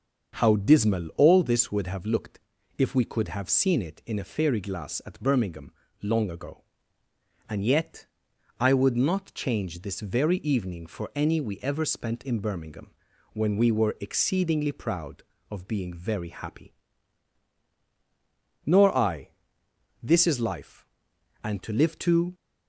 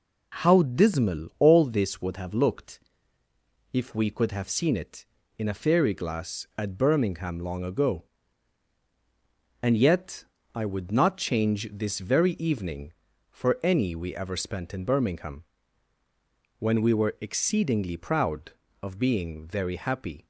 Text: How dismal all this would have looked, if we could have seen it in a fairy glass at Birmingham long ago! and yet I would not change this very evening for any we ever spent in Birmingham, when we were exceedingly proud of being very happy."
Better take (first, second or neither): second